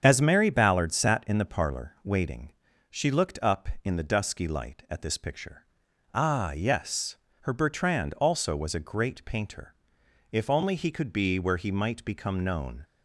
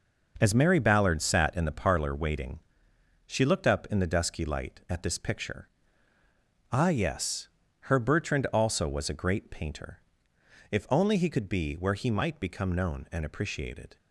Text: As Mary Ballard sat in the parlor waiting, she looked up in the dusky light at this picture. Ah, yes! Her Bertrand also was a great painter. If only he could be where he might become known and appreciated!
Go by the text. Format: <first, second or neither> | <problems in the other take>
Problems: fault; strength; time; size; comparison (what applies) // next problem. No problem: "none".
second | starts louder than the rest; strong; until 1.0 s; 7.5 dB // stops before "and appreciated"; at 12.8 s